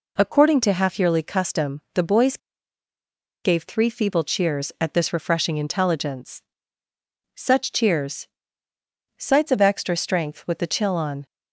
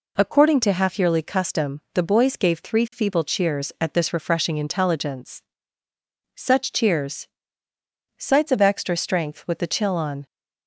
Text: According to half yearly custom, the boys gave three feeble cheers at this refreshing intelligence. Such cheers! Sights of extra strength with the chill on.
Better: second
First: pauses between "boys" and "gave"; at 2.3 s; 1.0 s long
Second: none

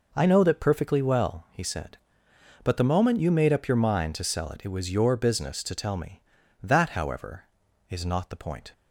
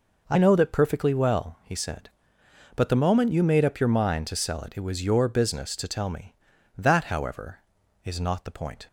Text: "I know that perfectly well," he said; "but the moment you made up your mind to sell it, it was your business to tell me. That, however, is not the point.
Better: neither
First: none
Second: none

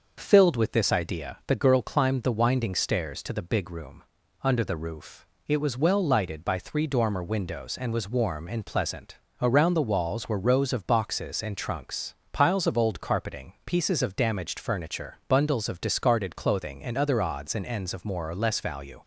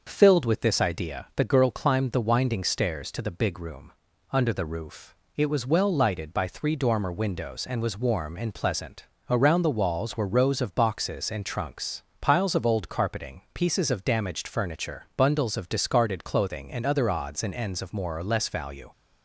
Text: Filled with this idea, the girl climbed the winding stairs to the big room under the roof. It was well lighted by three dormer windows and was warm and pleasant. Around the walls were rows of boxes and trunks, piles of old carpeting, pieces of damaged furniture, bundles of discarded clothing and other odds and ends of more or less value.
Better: neither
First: pauses between "room" and "under"; at 4.0 s; 0.40 s long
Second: pauses between "room" and "under"; at 3.9 s; 0.40 s long

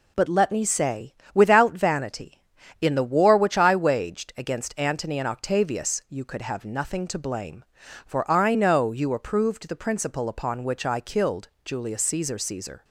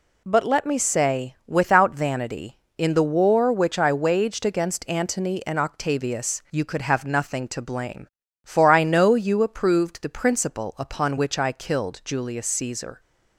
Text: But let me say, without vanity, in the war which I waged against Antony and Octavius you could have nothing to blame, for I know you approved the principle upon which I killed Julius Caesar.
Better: second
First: pauses between "killed" and "Julius"; slight; at 11.4 s; 0.16 s long // says "Caesar" twice; at 12.3 s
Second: none

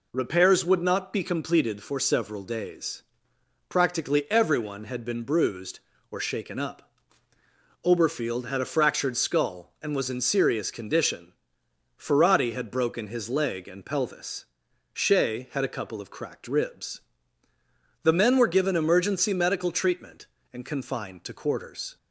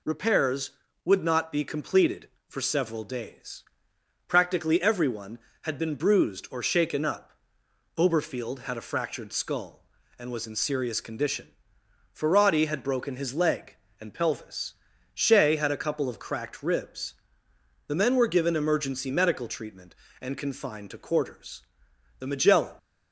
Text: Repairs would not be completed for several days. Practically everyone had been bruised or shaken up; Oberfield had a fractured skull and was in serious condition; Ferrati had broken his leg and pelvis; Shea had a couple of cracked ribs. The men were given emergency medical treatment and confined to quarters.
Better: first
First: none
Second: goes on to say "The Magellan"; from 22.1 s on; 0.56 s long

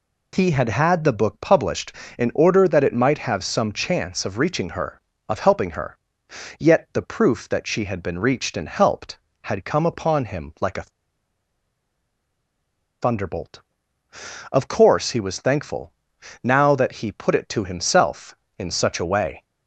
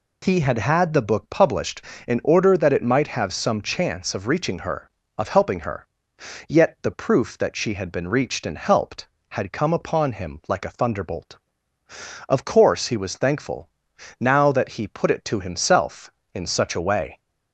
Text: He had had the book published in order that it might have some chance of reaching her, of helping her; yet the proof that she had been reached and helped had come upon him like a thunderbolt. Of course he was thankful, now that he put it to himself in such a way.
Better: second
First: pauses between "a" and "thunderbolt"; strong; at 10.8 s; 2.1 s long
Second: none

